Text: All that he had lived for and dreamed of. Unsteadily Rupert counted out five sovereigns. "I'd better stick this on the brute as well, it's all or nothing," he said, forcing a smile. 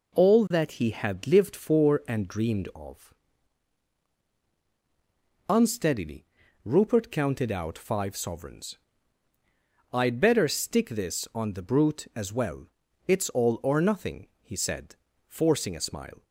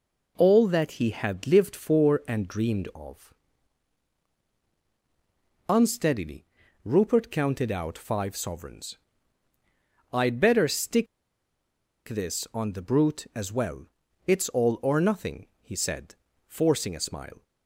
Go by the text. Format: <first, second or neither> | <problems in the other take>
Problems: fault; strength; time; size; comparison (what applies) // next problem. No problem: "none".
first | pauses between "Unsteadily" and "Rupert"; at 6.4 s; 0.38 s long; also in the first // pauses between "stick" and "this"; at 11.0 s; 1.0 s long